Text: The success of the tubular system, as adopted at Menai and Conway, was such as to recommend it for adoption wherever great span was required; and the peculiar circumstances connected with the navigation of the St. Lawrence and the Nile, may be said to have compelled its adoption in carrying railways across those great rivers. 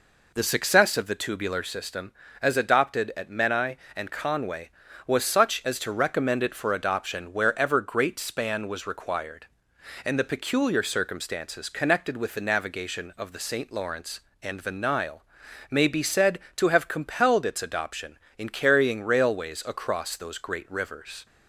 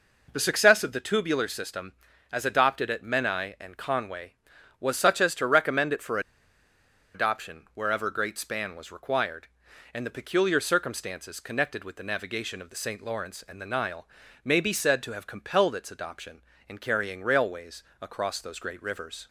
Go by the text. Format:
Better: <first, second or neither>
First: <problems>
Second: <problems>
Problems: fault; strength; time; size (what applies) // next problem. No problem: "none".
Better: first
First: none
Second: pauses between "for" and "adoption"; noticeable; at 6.1 s; 0.95 s long // pauses between "railways" and "across"; slight; at 17.8 s; 0.18 s long